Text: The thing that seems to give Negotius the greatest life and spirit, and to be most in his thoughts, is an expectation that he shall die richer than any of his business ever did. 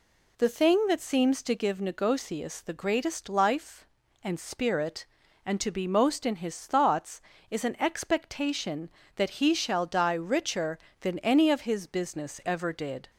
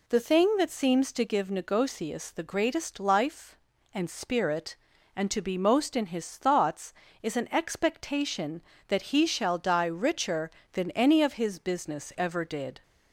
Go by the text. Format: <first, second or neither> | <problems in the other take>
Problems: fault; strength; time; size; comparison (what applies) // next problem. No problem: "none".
neither | none